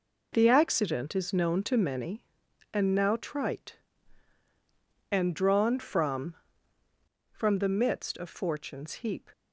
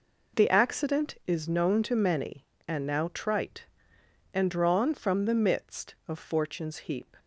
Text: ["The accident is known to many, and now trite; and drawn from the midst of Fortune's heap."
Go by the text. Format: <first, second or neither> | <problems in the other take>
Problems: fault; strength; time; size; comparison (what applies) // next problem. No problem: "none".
second | says "from" twice; at 7.2 s